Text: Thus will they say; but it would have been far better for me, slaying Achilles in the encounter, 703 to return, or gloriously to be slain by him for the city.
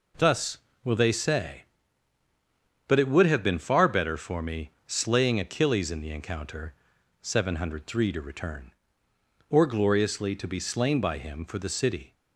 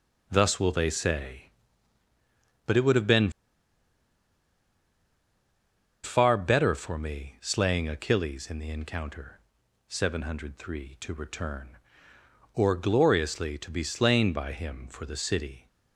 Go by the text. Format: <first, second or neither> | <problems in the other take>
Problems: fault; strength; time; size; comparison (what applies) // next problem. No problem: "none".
first | pauses between "been" and "far"; strong; at 3.2 s; 2.7 s long